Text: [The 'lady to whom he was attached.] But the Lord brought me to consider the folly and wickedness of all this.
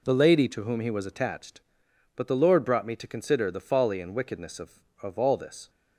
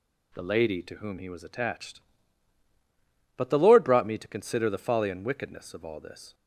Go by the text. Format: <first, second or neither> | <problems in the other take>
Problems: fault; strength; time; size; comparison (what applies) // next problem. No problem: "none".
second | says "of" twice; at 5.0 s